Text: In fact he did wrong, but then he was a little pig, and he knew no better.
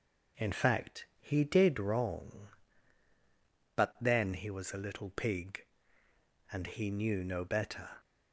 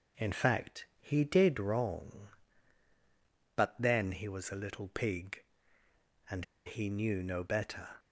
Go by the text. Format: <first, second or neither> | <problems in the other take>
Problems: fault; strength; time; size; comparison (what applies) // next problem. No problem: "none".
first | pauses between "and" and "he"; slight; at 6.4 s; 0.21 s long